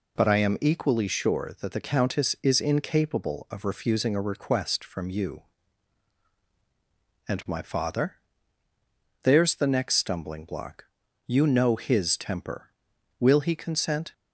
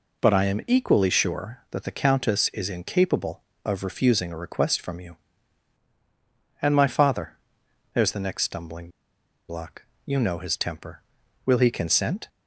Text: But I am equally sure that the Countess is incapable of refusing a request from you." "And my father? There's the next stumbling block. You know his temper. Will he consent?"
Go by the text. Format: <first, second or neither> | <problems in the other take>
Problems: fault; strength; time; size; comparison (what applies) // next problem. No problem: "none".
first | pauses between "stumbling" and "block"; noticeable; at 8.8 s; 0.60 s long